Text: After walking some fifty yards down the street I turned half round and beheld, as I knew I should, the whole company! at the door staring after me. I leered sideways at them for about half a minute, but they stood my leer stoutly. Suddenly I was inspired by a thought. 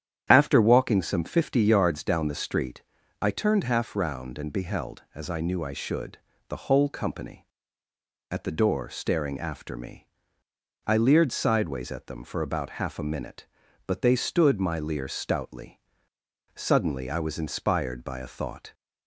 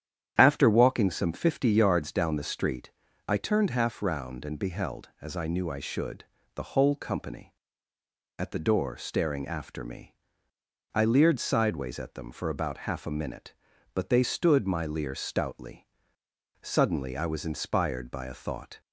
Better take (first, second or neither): neither